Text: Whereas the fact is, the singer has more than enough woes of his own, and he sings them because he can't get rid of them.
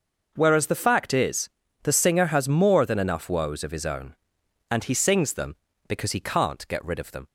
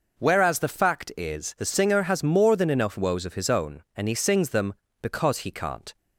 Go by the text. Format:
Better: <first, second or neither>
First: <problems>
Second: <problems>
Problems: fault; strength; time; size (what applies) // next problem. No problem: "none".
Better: first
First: none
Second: stops before "get rid of them"; at 5.9 s